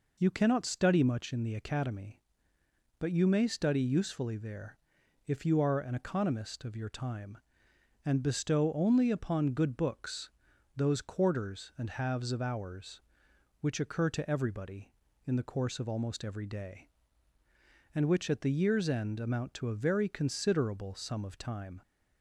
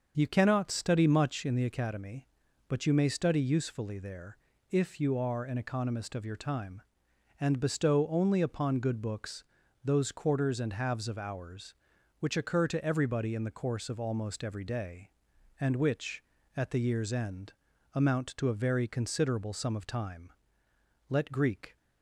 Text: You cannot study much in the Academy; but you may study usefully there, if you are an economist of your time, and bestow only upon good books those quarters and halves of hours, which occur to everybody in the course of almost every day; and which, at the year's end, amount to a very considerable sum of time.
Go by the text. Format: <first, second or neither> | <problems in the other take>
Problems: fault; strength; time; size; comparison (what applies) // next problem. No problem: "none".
first | starts louder than the rest; until 1.1 s; 6.5 dB // pauses between "books" and "those"; at 9.4 s; 0.40 s long; also in the first // goes on to say "Let Greek"; noticeable; from 21.0 s on; 0.66 s long